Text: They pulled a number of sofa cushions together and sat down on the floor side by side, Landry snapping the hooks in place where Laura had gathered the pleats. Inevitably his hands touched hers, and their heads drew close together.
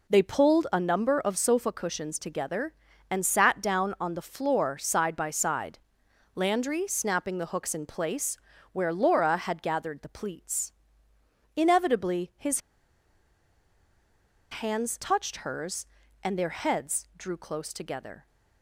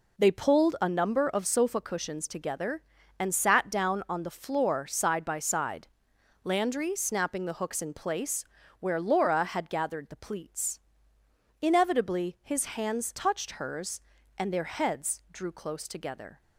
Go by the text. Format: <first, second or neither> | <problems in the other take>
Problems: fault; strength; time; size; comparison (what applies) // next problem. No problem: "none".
second | pauses between "place" and "where"; slight; at 8.3 s; 0.34 s long; slight in the second // pauses between "his" and "hands"; strong; at 12.5 s; 1.9 s long